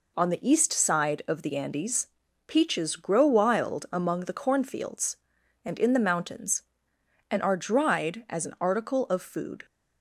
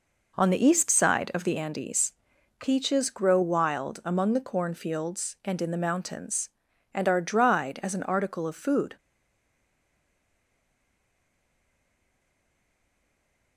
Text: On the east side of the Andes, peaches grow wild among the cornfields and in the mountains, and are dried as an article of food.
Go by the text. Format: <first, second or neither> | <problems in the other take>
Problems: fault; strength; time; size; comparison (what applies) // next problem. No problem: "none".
first | stays silent after the last word; strong; from 8.9 s on; 4.6 s long